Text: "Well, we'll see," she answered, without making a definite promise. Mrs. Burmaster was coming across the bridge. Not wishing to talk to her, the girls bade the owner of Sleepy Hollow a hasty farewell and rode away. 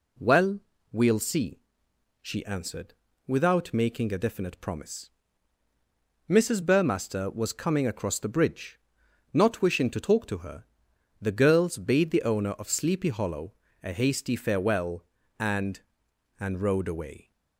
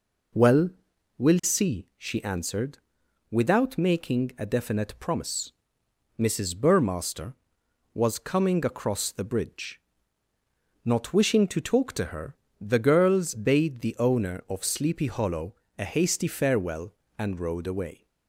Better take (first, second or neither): second